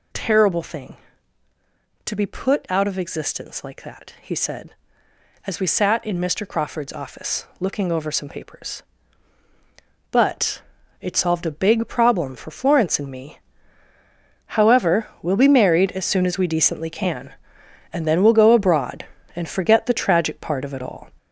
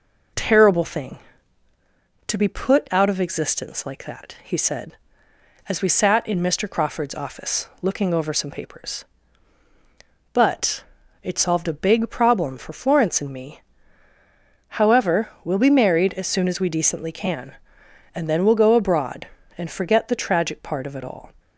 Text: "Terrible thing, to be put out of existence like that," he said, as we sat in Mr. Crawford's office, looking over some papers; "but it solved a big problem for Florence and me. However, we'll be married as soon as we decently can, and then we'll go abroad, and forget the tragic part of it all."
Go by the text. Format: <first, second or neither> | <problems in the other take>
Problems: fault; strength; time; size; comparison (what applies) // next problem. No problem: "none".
second | gets louder; throughout; 7 dB // pauses between "but" and "it"; at 10.6 s; 0.40 s long; also in the second